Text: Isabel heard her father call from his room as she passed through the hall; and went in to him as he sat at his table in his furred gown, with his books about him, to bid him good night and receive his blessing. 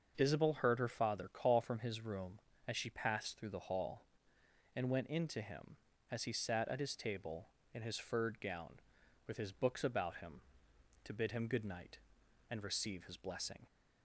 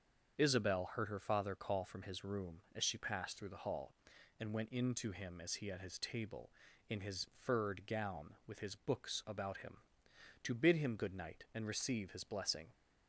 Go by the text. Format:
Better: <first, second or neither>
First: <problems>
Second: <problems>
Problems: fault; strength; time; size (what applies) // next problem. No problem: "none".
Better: first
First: starts louder than the rest; until 1.1 s; 6.5 dB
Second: starts louder than the rest; until 1.4 s; 7 dB // skips "sat"; at 5.7 s